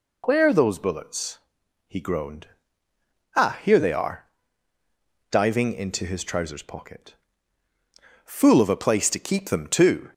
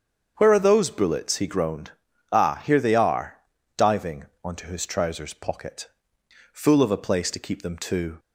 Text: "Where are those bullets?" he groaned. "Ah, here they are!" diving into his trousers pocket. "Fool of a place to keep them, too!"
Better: first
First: none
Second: starts louder than the rest; strong; until 1.3 s; 7.5 dB // says "onto" for "into"; at 4.4 s

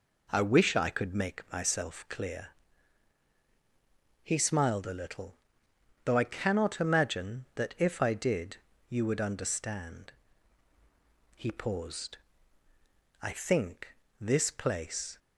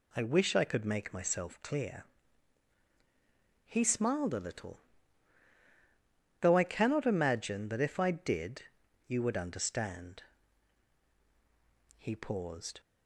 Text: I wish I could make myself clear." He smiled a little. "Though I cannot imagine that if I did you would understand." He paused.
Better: second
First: pauses between "did" and "you"; slight; at 8.5 s; 0.32 s long // goes on to say "I think this place"; strong; from 13.2 s on; 1.9 s long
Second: pauses between "did" and "you"; at 8.6 s; 0.42 s long

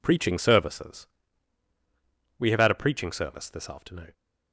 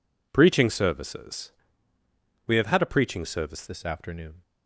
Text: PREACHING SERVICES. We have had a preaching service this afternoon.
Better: first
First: none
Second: changes voice at "this"; from 3.6 s on; 0.8 s long

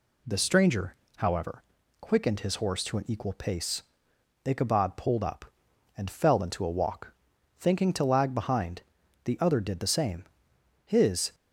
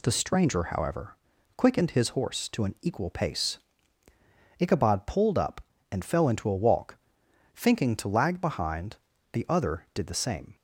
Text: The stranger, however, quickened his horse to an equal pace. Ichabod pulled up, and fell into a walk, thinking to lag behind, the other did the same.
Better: second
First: goes on to say "His"; from 10.8 s on; 0.50 s long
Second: none

